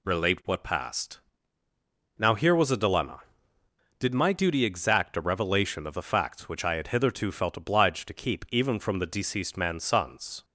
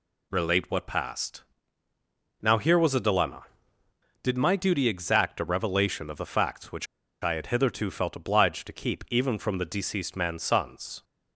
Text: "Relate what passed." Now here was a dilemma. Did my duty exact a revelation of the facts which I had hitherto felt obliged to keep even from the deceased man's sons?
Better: first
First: none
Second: pauses between "which" and "I"; slight; at 6.8 s; 0.35 s long

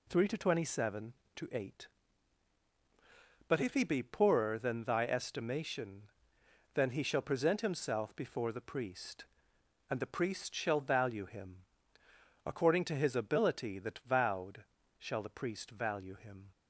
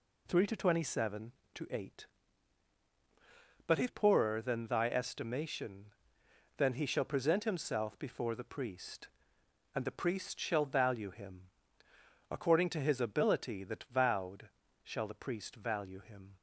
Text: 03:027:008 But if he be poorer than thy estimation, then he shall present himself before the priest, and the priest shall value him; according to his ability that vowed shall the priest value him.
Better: first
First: pauses between "vowed" and "shall"; at 14.6 s; 0.38 s long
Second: skips "he be"; at 3.8 s // pauses between "vowed" and "shall"; at 14.4 s; 0.38 s long

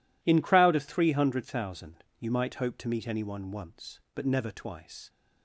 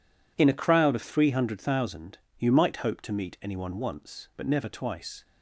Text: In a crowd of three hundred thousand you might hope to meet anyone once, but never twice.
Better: second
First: skips "a"; at 0.4 s // pauses between "thousand" and "you"; slight; at 2.0 s; 0.16 s long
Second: pauses between "thousand" and "you"; slight; at 2.1 s; 0.22 s long

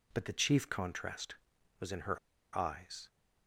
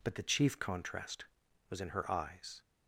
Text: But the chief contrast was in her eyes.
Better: second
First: pauses between "her" and "eyes"; at 2.1 s; 0.37 s long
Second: none

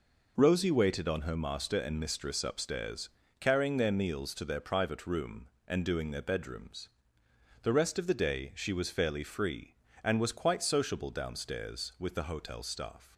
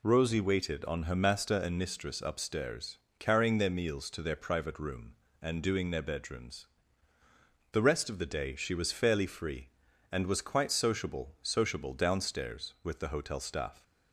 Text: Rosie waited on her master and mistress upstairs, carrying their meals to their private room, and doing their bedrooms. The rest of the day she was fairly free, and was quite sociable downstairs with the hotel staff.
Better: first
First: none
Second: says "sociable" twice; at 11.4 s

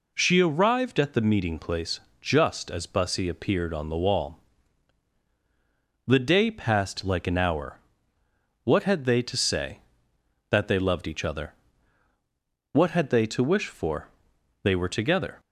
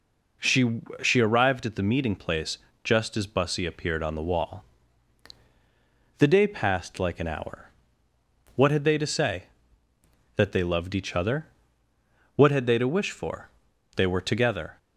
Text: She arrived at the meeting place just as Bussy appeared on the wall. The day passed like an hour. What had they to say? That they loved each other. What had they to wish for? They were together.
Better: first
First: pauses between "place" and "just"; slight; at 1.9 s; 0.22 s long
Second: says "She" twice; at 1.0 s // pauses between "place" and "just"; slight; at 2.5 s; 0.24 s long

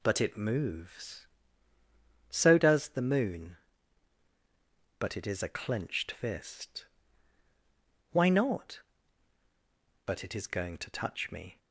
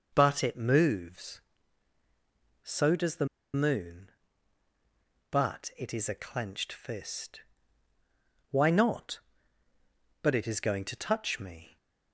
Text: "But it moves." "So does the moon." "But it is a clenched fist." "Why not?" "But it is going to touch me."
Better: first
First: none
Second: pauses between "the" and "moon"; slight; at 3.2 s; 0.28 s long

